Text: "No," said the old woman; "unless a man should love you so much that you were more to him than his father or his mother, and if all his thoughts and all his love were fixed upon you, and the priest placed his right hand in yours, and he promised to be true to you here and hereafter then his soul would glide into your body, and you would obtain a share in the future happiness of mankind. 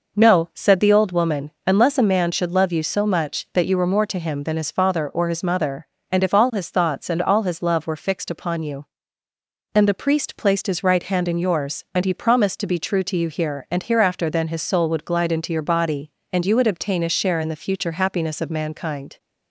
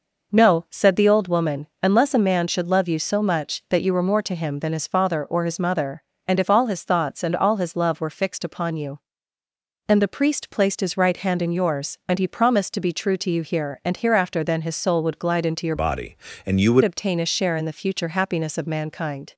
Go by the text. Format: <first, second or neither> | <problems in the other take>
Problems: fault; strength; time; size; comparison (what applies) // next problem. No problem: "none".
first | changes voice from "body" to "would"; from 15.7 to 16.8 s; 1.1 s long